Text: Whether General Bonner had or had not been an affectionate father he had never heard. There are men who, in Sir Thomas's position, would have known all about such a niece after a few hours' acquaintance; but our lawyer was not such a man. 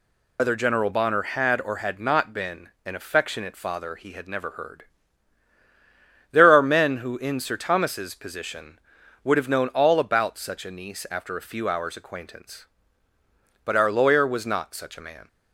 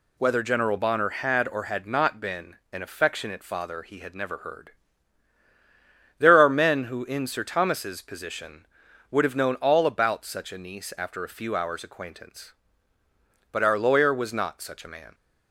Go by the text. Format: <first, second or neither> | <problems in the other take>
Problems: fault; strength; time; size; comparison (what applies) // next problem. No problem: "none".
second | loses the start of "Whether"; at 0.3 s; 85 ms // pauses between "been" and "an"; slight; at 2.6 s; 0.16 s long; slight in the second